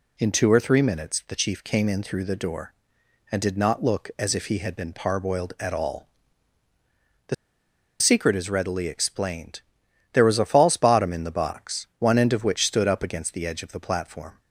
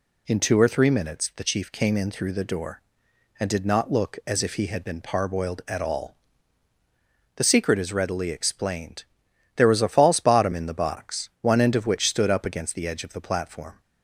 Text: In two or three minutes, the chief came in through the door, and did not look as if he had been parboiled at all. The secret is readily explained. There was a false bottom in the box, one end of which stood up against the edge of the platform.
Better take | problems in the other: second | pauses between "The" and "secret"; noticeable; at 7.3 s; 0.66 s long

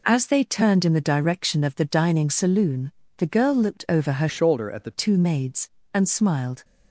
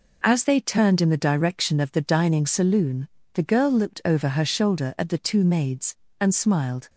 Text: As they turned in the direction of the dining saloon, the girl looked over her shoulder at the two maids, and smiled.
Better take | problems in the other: second | changes voice from "shoulder" to "the"; from 4.2 to 4.9 s; 0.7 s long

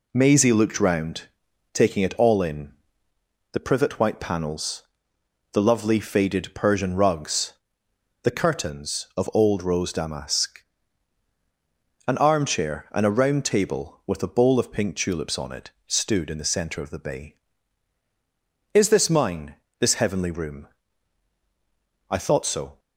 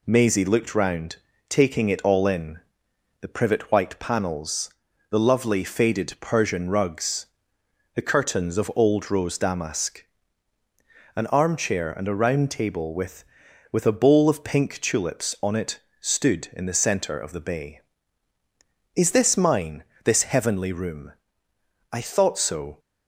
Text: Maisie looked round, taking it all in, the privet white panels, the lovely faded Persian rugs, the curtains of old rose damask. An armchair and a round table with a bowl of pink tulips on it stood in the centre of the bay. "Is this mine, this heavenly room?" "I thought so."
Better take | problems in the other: first | says "with" twice; at 13.7 s // pauses between "it" and "stood"; slight; at 15.7 s; 0.20 s long; slight in the first

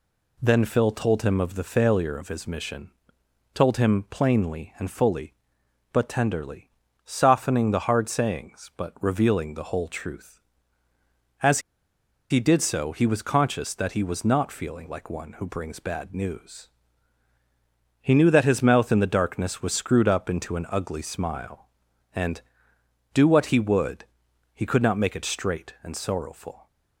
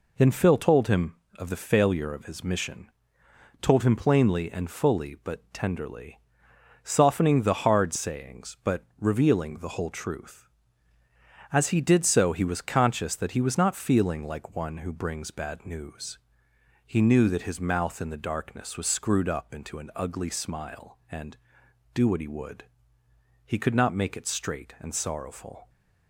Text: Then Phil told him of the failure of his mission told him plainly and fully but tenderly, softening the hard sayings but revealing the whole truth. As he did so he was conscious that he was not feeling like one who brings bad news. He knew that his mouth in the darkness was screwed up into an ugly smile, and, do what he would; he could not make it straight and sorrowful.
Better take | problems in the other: second | pauses between "mission" and "told"; noticeable; at 2.9 s; 0.64 s long; noticeable in the second // pauses between "As" and "he"; noticeable; at 11.5 s; 0.71 s long

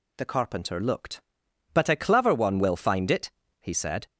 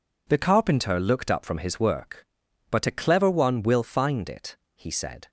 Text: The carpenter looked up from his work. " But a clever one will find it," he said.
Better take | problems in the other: second | skips "up from his work"; at 1.3 s

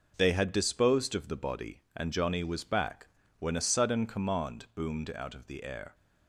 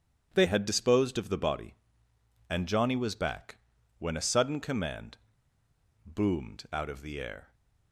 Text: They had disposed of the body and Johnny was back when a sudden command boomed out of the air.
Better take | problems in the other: first | starts louder than the rest; strong; until 1.3 s; 9 dB // pauses between "back" and "when"; at 3.5 s; 0.42 s long; slight in the first // pauses between "command" and "boomed"; noticeable; at 5.1 s; 0.87 s long

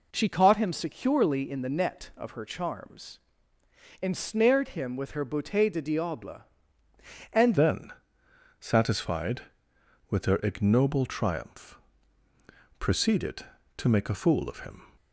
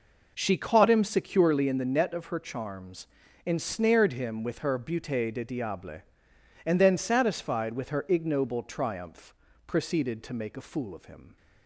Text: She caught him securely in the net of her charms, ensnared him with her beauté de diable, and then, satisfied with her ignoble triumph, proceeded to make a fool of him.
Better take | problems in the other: second | changes voice at "then"; from 7.5 s on; 7.3 s long

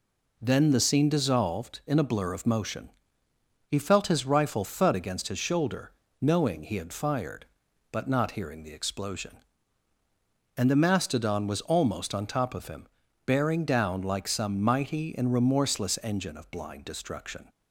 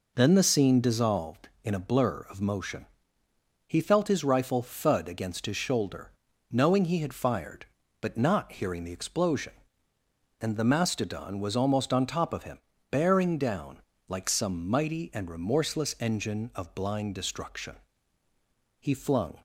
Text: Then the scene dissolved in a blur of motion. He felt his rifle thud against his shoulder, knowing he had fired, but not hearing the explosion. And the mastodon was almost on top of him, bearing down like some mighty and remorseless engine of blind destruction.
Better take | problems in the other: first | pauses between "down" and "like"; slight; at 13.8 s; 0.26 s long // goes on to say "He flung"; from 18.8 s on; 0.58 s long

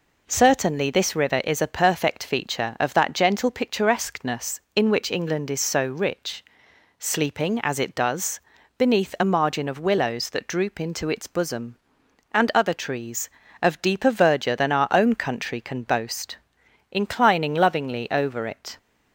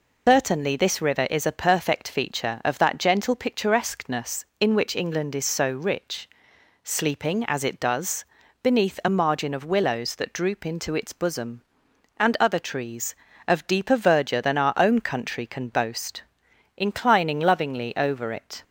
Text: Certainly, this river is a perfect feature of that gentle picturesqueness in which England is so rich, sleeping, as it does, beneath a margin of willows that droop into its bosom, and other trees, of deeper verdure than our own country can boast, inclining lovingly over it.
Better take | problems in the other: first | loses the start of "Certainly"; at 0.2 s; 135 ms

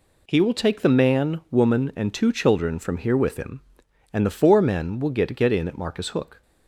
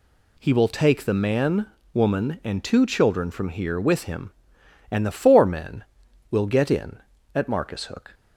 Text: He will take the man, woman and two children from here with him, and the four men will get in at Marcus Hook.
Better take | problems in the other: second | says "get" twice; at 5.3 s

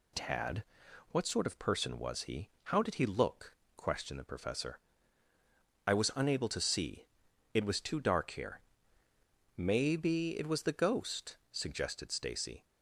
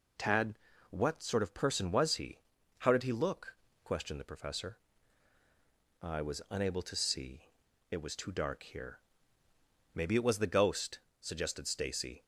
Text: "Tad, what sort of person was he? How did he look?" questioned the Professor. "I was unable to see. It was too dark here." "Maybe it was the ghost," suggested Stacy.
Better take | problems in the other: neither | none

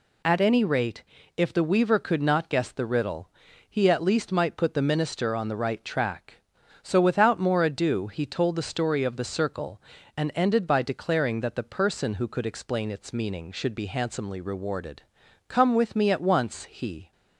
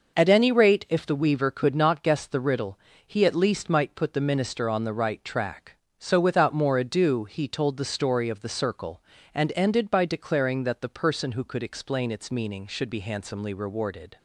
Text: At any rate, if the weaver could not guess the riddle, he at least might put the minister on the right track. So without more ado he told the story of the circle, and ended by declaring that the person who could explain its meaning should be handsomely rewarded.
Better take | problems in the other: second | goes on to say "Come with me at once he"; from 15.4 s on; 1.6 s long

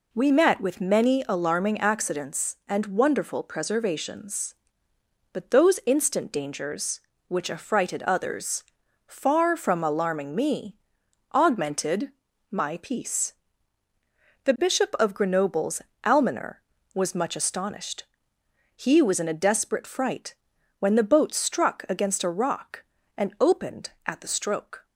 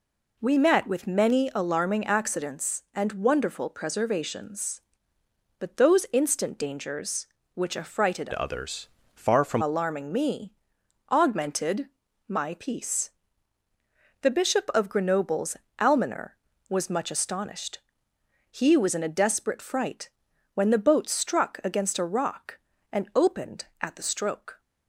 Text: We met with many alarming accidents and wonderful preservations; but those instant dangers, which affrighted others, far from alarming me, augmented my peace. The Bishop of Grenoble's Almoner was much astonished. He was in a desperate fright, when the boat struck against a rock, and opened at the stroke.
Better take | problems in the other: first | changes voice from "others" to "from"; from 8.3 to 9.6 s; 1.3 s long // pauses between "augmented" and "my"; at 11.8 s; 0.40 s long; also in the first // pauses between "Grenoble's" and "Almoner"; slight; at 15.5 s; 0.22 s long; slight in the first

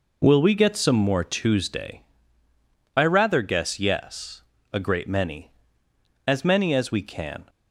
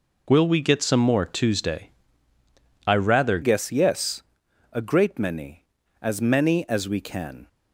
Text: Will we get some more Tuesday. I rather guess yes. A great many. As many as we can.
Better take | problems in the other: first | changes voice at "guess"; from 3.4 s on; 4.0 s long

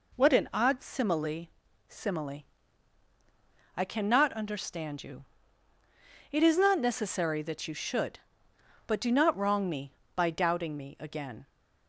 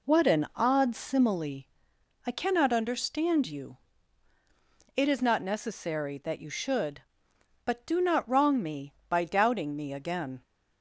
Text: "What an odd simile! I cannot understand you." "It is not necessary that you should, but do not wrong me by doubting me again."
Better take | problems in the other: second | says "simile" twice; at 1.8 s

